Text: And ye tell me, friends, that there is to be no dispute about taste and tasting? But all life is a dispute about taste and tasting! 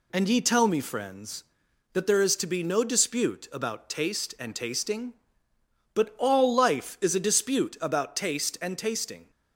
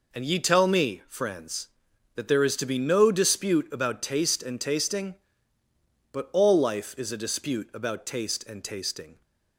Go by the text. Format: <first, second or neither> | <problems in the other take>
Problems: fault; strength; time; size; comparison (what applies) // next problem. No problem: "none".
neither | none